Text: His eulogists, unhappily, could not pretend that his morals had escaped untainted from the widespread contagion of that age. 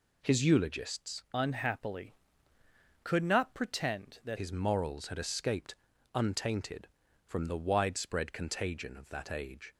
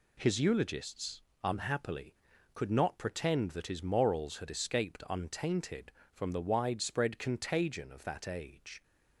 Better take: second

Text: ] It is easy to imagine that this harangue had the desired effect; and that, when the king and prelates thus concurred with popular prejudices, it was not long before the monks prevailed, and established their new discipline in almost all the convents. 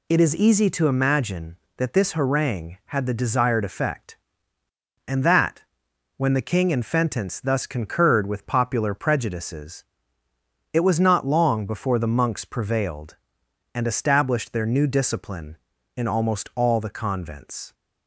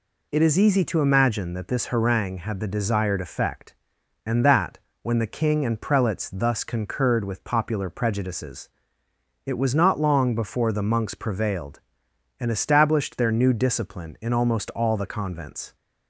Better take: second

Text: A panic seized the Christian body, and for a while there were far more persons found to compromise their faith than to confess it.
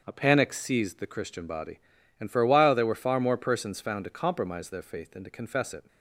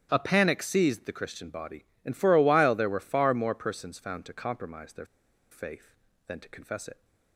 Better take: first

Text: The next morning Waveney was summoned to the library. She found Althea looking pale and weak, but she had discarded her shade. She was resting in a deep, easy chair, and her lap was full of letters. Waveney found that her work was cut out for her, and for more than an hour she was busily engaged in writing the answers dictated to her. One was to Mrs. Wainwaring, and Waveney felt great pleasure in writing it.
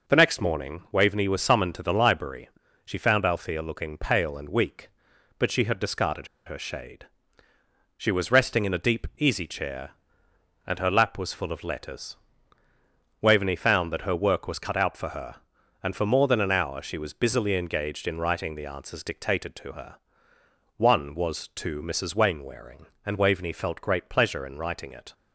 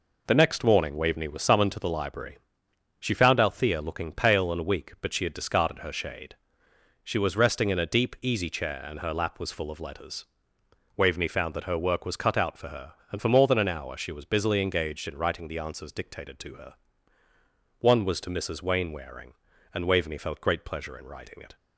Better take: second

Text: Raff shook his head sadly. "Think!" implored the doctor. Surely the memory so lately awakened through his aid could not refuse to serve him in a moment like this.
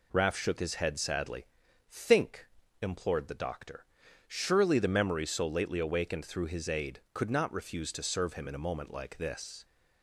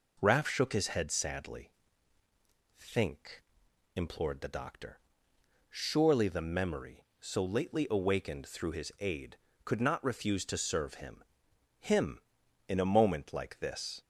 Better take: first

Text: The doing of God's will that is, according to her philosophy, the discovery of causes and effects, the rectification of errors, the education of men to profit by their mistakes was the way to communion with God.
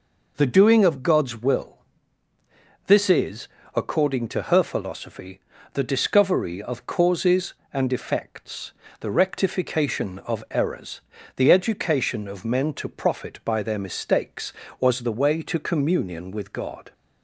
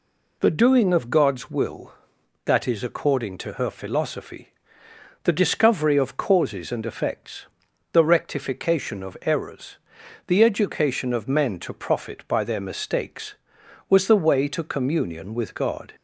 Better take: second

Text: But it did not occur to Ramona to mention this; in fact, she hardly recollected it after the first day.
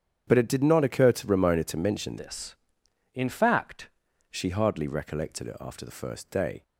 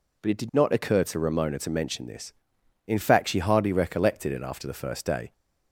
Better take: second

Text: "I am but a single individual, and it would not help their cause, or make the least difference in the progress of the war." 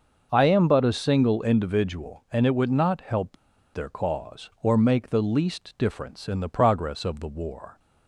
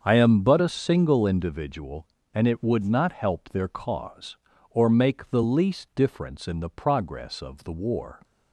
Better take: second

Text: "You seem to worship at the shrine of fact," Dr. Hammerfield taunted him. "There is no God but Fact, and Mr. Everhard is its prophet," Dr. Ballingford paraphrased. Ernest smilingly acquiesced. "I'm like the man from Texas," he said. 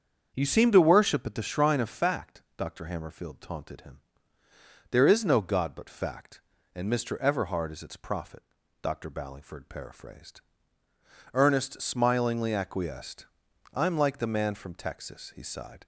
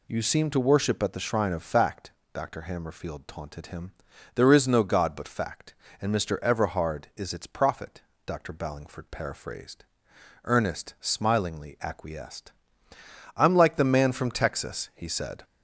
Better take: second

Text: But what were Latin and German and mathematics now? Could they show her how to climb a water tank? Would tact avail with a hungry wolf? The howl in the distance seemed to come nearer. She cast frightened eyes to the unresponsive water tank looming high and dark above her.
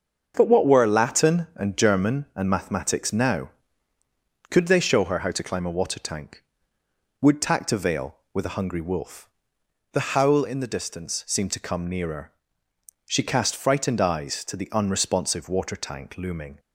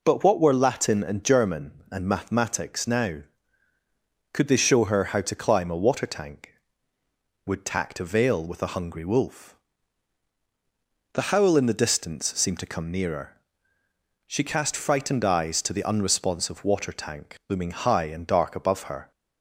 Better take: second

